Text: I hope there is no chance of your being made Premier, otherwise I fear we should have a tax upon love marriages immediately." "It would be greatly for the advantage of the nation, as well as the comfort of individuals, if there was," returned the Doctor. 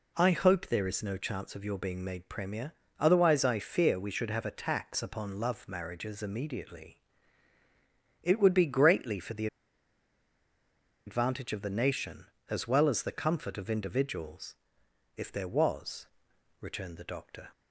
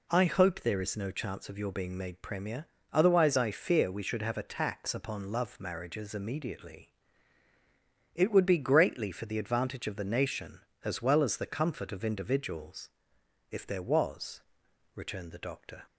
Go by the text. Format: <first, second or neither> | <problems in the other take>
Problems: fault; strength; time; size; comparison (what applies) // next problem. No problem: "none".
second | pauses between "the" and "advantage"; strong; at 9.4 s; 1.5 s long